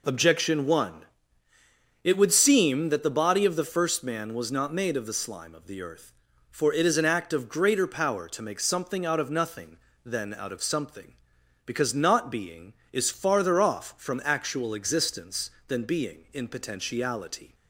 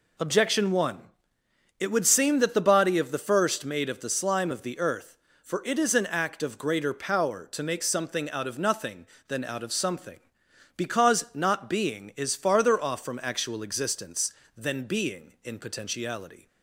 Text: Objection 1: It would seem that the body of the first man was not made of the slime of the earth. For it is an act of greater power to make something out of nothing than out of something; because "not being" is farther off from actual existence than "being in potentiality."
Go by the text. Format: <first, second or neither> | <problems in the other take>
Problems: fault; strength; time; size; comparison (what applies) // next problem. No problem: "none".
first | skips "man was not"; at 3.6 s